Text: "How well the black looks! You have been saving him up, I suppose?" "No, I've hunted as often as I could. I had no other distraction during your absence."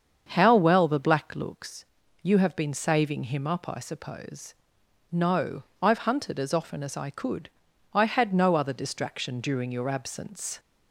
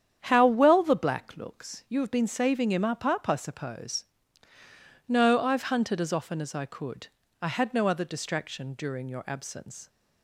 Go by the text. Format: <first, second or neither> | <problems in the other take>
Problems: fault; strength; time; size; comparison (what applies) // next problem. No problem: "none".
first | starts louder than the rest; strong; until 1.2 s; 9 dB; strong in the first // says "up" twice; at 3.0 s